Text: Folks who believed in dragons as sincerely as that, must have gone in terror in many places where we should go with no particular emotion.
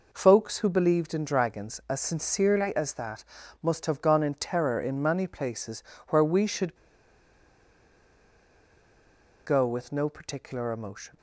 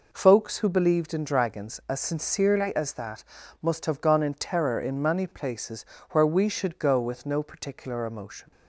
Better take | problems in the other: second | pauses between "places" and "where"; slight; at 5.8 s; 0.26 s long; slight in the second // pauses between "should" and "go"; strong; at 6.7 s; 2.6 s long

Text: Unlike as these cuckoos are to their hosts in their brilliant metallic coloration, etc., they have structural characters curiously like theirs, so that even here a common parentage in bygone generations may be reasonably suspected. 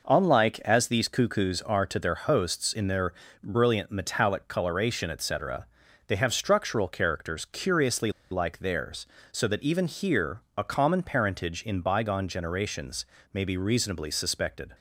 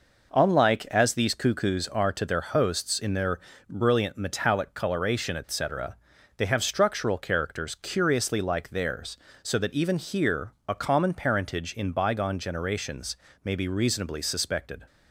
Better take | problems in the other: second | pauses between "their" and "brilliant"; slight; at 3.1 s; 0.30 s long; slight in the second // pauses between "curiously" and "like"; slight; at 8.1 s; 0.20 s long // pauses between "here" and "a"; slight; at 10.4 s; 0.16 s long; slight in the second // pauses between "generations" and "may"; slight; at 13.0 s; 0.26 s long; slight in the second

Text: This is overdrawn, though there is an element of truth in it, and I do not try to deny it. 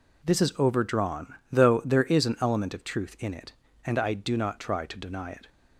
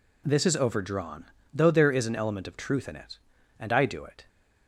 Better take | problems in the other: first | skips "not try to deny"; at 4.0 s

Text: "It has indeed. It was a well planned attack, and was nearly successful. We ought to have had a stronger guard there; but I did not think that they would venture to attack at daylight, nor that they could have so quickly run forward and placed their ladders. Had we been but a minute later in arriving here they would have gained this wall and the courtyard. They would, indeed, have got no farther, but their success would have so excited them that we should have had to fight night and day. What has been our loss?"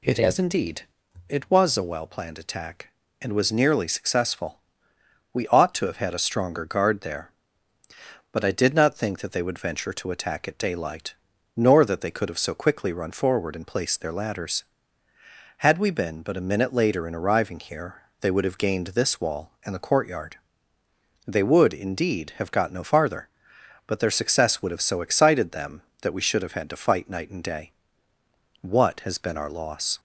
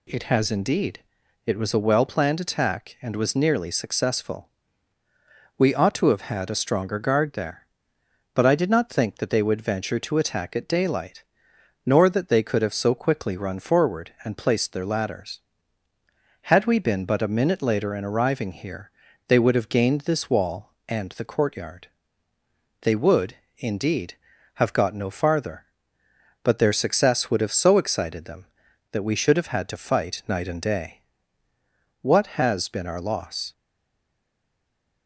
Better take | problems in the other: first | pauses between "here" and "they"; at 18.9 s; 0.38 s long; slight in the first // stays silent after the last word; noticeable; from 33.5 s on; 1.5 s long

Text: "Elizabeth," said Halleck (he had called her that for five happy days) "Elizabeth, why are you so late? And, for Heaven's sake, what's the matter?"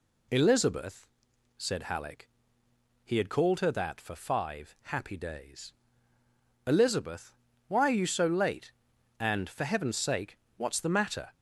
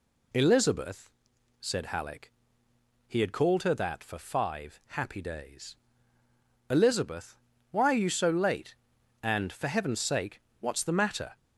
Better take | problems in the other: neither | none

